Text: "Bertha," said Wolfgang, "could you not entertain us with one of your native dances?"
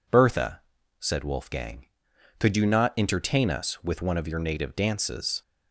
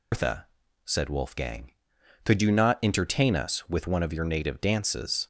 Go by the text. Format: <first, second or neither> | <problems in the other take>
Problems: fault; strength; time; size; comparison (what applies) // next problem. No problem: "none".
first | loses the start of "Bertha"; at 0.1 s; 170 ms